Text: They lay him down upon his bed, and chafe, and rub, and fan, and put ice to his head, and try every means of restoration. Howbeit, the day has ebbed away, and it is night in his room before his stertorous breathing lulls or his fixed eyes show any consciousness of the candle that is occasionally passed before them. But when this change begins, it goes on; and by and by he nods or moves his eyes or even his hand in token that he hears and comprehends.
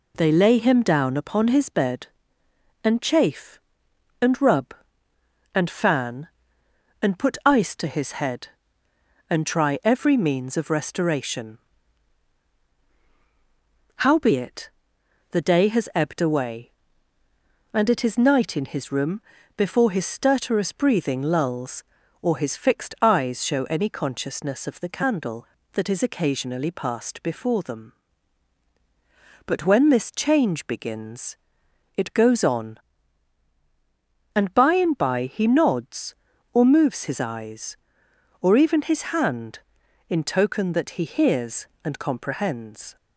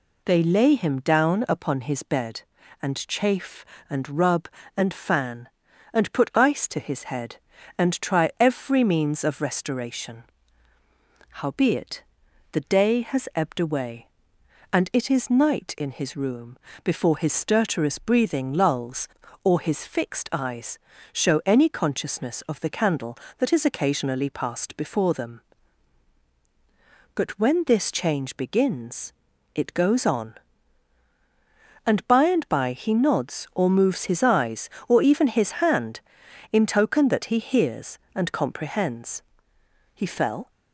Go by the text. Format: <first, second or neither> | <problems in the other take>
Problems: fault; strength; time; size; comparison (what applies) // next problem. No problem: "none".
first | pauses between "room" and "before"; slight; at 16.5 s; 0.28 s long; slight in the first // pauses between "eyes" and "show"; slight; at 20.7 s; 0.34 s long // goes on to say "He fell"; from 39.9 s on; 0.56 s long